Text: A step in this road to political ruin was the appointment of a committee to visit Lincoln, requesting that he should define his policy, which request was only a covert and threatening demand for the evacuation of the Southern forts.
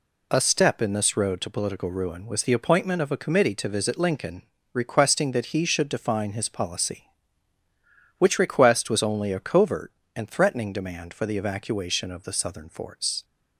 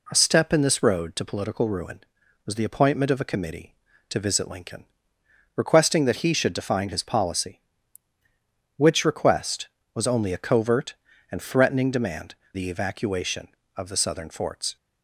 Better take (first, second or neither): first